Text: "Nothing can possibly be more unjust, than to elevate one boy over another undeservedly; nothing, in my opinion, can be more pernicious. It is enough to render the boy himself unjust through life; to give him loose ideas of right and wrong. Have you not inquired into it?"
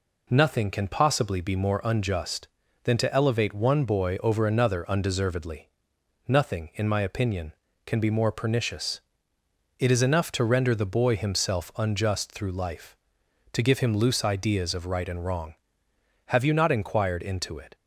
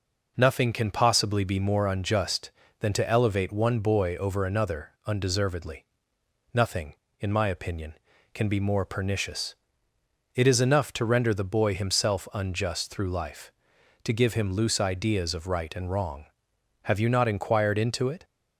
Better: neither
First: none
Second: none

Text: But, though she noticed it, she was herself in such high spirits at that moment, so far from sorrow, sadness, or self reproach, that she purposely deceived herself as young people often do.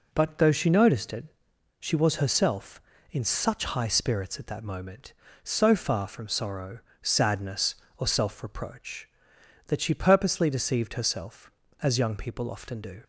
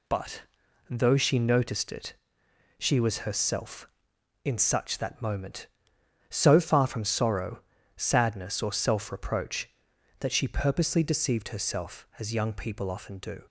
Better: first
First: none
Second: skips "high spirits at"; at 4.9 s

